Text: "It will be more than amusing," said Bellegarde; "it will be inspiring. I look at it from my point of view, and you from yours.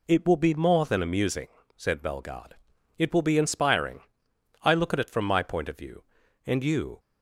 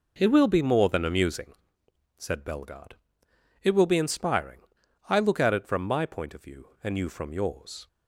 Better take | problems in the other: second | stops before "from yours"; at 6.9 s

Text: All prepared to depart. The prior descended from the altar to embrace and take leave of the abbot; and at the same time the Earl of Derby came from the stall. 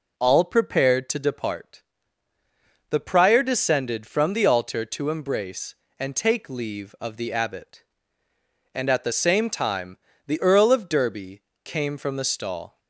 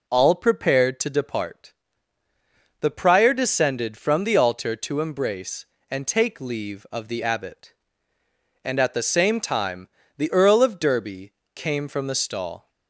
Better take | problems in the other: neither | pauses between "time" and "the"; slight; the same in both // pauses between "Derby" and "came"; slight; the same in both

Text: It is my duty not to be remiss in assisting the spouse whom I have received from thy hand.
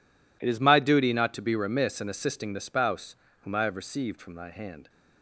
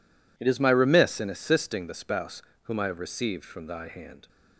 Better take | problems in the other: first | skips "duty not to be"; at 0.6 s // pauses between "spouse" and "whom"; slight; at 2.4 s; 0.22 s long; slight in the first

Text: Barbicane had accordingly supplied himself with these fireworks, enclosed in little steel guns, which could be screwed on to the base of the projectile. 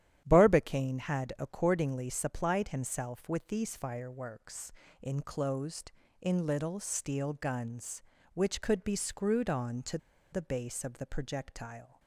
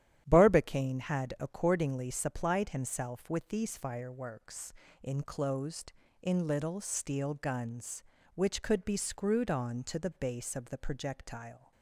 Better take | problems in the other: second | starts louder than the rest; strong; until 1.2 s; 11 dB; strong in the second // pauses between "to" and "the"; slight; at 9.9 s; 0.35 s long

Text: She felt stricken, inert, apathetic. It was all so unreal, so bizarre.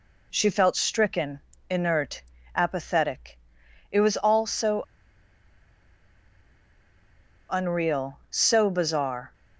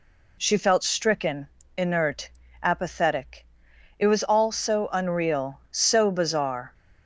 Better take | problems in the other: second | pauses between "so" and "unreal"; strong; at 4.8 s; 2.6 s long

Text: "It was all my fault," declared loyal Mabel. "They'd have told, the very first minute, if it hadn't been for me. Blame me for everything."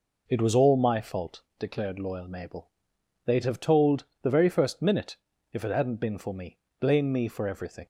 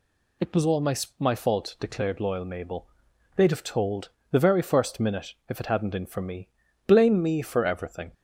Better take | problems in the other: first | says "my" twice; at 1.1 s

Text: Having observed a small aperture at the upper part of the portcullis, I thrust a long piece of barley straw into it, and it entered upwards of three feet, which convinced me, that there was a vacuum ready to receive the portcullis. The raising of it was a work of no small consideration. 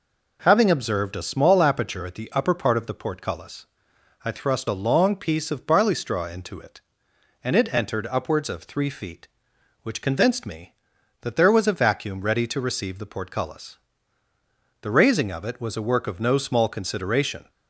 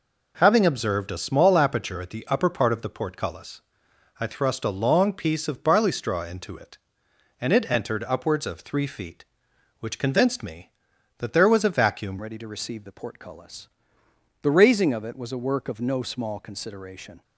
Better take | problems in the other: first | changes voice at "ready"; from 12.2 s on; 5.0 s long

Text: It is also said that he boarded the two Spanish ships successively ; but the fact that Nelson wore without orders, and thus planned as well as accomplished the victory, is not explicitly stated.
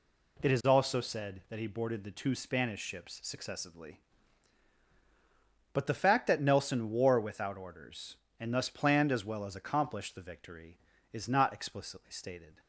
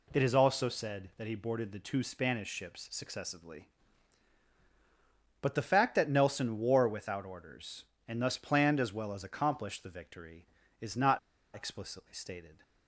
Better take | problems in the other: first | pauses between "not" and "explicitly"; slight; at 11.1 s; 0.35 s long

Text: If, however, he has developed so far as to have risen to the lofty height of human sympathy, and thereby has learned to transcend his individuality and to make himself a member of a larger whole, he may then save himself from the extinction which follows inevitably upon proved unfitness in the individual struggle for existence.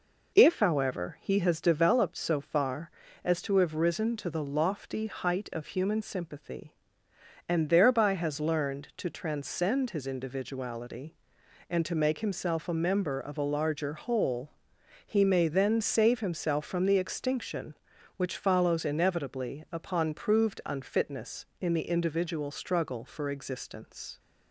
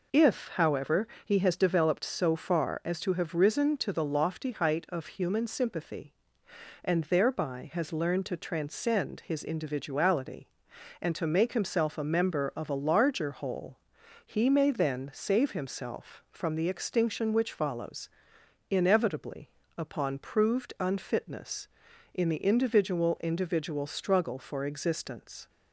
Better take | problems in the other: first | pauses between "follows" and "inevitably"; noticeable; at 18.0 s; 0.60 s long // pauses between "inevitably" and "upon"; slight; at 19.4 s; 0.26 s long // says "individual" twice; at 23.2 s

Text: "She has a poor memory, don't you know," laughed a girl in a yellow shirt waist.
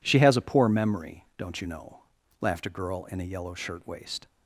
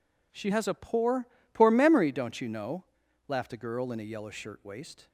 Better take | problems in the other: first | says "poor" twice; at 1.5 s

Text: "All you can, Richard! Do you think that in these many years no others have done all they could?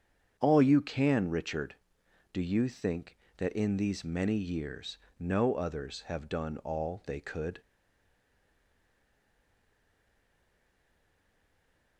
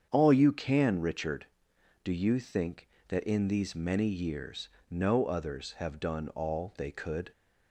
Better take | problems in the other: second | starts louder than the rest; strong; until 1.4 s; 7.5 dB; strong in the second // pauses between "years" and "no"; slight; at 4.9 s; 0.18 s long; slight in the second // stays silent after the last word; strong; from 7.6 s on; 4.3 s long

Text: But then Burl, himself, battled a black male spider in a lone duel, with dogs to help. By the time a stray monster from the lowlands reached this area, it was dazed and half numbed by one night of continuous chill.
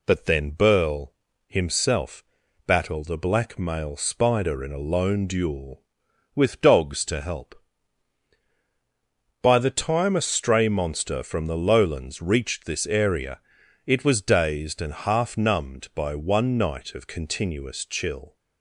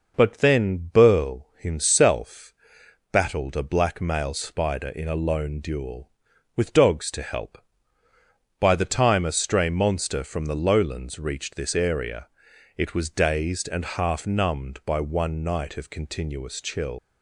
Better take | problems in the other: first | leaves "chill" unfinished; at 16.9 s; 85 ms

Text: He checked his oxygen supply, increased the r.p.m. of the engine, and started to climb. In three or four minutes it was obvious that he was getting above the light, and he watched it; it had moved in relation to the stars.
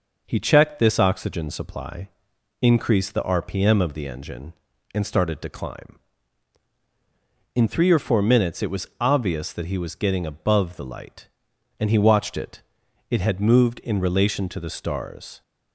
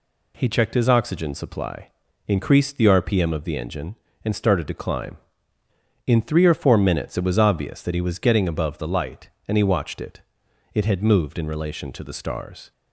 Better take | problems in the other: second | says "this" for "his"; at 0.7 s

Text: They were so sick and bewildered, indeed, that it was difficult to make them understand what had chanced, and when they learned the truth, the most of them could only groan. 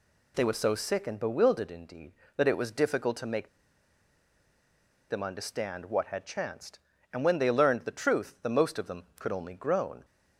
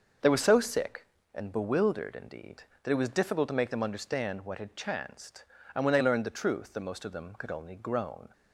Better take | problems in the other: second | pauses between "make" and "them"; strong; at 3.4 s; 1.6 s long

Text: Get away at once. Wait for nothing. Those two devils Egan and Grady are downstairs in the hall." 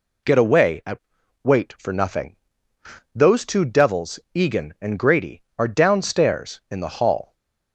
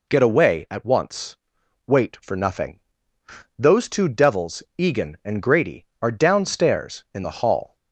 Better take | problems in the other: second | skips "once"; at 1.2 s // stays silent after the last word; slight; from 7.2 s on; 0.5 s long

